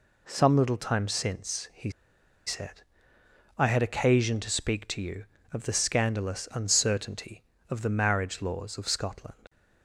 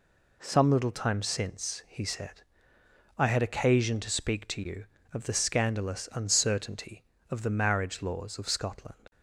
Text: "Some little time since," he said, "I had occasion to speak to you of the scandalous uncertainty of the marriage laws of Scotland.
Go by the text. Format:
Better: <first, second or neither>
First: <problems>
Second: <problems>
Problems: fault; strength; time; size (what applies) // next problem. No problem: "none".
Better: second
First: pauses between "he" and "said"; noticeable; at 1.9 s; 0.54 s long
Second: none